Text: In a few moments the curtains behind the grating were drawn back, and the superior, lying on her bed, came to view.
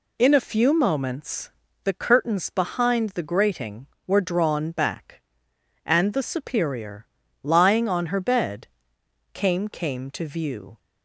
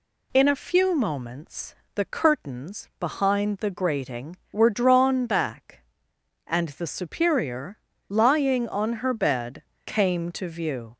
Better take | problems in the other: second | pauses between "moments" and "the"; slight; at 1.4 s; 0.34 s long; slight in the second // says "came" twice; at 9.6 s

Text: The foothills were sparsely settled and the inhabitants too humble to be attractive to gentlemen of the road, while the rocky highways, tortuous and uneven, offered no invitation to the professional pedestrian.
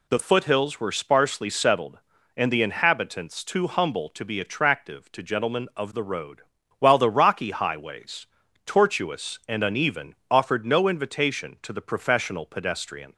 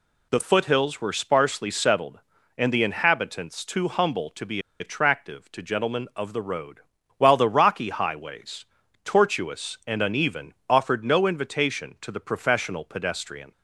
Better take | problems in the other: first | pauses between "be" and "attractive"; slight; at 4.6 s; 0.19 s long

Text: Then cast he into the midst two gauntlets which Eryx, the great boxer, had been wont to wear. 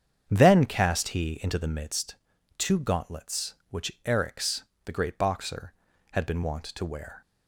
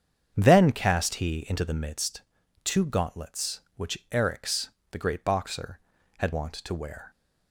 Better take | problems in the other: first | starts louder than the rest; strong; until 1.3 s; 8 dB; strong in the first // pauses between "midst" and "two"; at 2.2 s; 0.42 s long; also in the first // skips "been"; at 6.3 s

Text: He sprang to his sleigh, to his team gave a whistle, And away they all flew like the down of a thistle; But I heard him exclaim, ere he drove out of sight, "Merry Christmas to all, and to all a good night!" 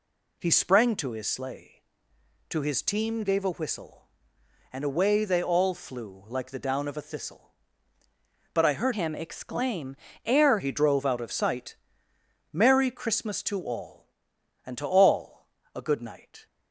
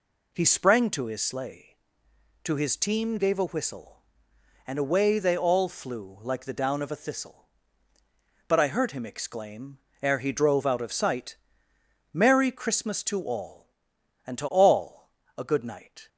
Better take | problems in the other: second | changes voice from "him" to "ere"; from 8.9 to 10.5 s; 1.6 s long // pauses between "all" and "a"; slight; at 15.4 s; 0.26 s long; slight in the second

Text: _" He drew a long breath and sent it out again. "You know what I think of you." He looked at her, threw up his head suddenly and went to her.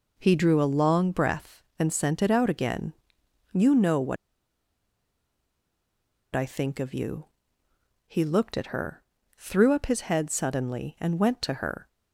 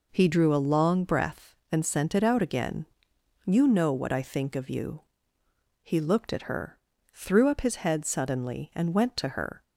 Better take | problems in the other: second | pauses between "what" and "I"; strong; at 4.1 s; 2.1 s long

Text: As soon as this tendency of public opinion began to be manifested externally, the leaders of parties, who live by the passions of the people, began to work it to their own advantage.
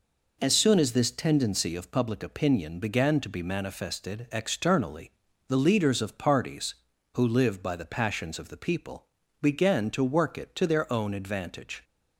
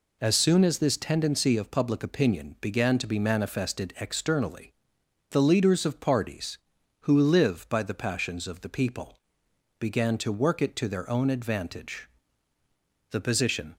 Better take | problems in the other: first | goes on to say "The position"; noticeable; from 13.0 s on; 0.66 s long

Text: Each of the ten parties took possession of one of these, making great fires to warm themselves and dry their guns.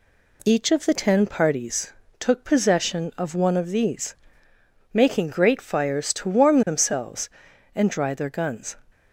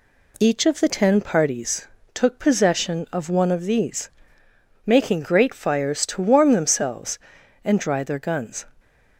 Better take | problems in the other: neither | pauses between "parties" and "took"; slight; the same in both

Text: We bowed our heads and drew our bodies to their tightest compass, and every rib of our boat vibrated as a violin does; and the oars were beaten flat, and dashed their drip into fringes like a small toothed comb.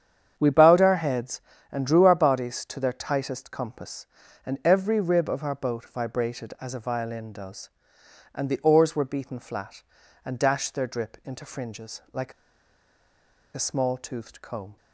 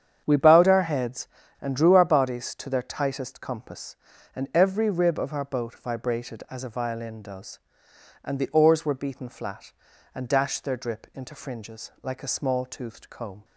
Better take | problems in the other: second | starts louder than the rest; strong; until 1.3 s; 8.5 dB; strong in the second // pauses between "like" and "a"; at 12.3 s; 1.2 s long

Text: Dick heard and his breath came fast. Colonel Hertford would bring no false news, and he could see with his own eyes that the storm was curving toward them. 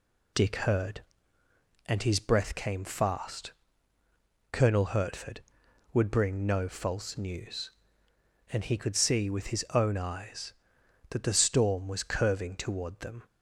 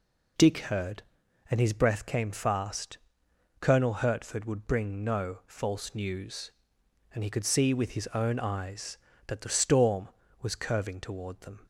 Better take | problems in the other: neither | none

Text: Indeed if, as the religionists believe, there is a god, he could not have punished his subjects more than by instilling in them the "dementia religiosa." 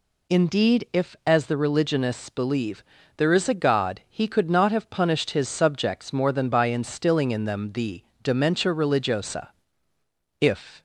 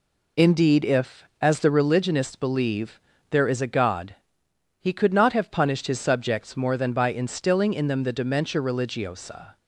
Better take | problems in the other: second | pauses between "the" and "dementia"; slight; at 8.0 s; 0.20 s long // goes on to say "If"; slight; from 10.3 s on; 0.42 s long

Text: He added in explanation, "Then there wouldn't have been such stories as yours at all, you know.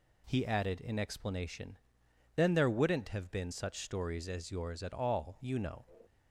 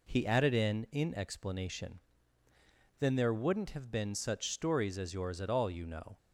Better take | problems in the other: first | says "in" twice; at 0.9 s

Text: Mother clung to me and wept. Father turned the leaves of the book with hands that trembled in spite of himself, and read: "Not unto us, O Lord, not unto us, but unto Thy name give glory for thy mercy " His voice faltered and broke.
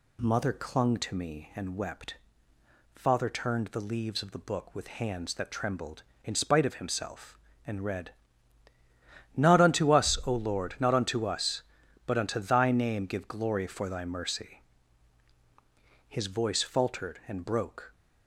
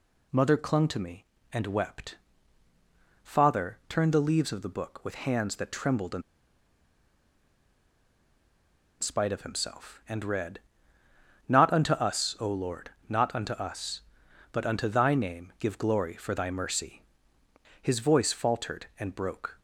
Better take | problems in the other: first | pauses between "in" and "spite"; strong; at 6.2 s; 2.7 s long

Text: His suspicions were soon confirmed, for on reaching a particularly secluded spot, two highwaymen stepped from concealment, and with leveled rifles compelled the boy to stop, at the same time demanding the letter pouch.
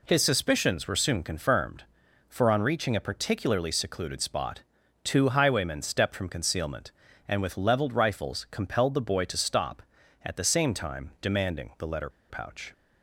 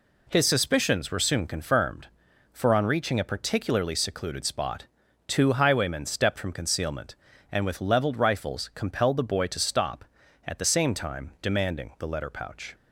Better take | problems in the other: second | pauses between "letter" and "pouch"; slight; at 12.0 s; 0.19 s long

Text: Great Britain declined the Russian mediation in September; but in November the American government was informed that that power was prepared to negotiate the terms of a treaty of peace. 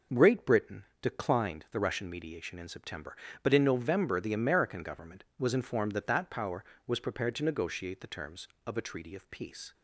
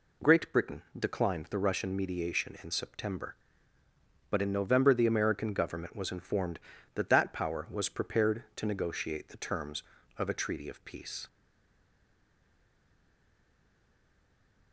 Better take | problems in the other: first | pauses between "Britain" and "declined"; slight; at 0.8 s; 0.16 s long; slight in the first // stays silent after the last word; strong; from 11.2 s on; 3.5 s long

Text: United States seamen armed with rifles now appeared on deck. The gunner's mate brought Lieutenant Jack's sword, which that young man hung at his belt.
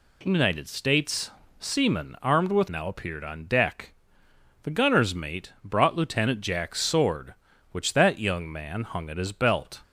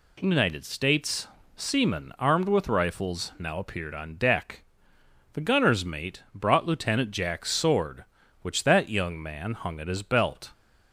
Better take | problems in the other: second | pauses between "States" and "seamen"; slight; at 1.3 s; 0.26 s long; slight in the second // skips "rifles"; at 2.6 s

